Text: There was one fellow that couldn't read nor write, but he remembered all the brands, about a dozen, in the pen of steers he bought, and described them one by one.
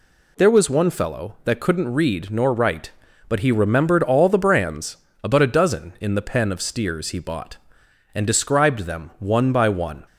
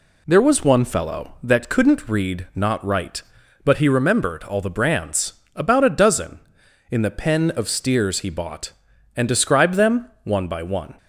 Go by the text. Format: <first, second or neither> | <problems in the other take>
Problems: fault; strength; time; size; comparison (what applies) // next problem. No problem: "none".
first | says "not" for "nor"; at 2.5 s